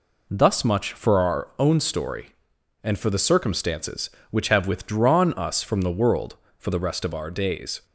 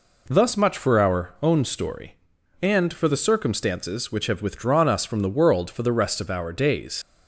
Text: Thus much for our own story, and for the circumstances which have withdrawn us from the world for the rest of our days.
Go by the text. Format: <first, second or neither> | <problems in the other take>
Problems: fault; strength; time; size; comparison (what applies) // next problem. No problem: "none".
first | leaves "days" unfinished; at 7.0 s; 90 ms